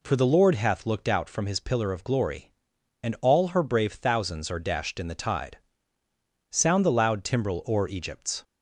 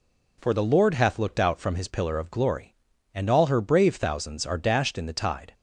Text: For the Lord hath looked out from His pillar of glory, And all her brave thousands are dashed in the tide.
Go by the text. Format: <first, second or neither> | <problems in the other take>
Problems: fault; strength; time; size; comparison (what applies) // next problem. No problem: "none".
second | goes on to say "Sound the loud timbrel o'er Egypt's"; strong; from 6.4 s on; 1.9 s long